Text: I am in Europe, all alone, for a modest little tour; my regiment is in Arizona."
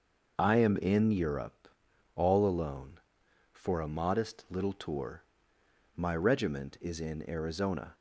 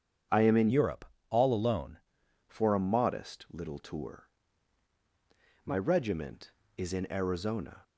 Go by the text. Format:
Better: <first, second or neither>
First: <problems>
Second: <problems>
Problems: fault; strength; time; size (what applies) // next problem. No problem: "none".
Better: first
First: none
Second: starts louder than the rest; strong; until 1.5 s; 7.5 dB // changes voice from "Europe" to "alone"; from 0.7 to 1.9 s; 1.2 s long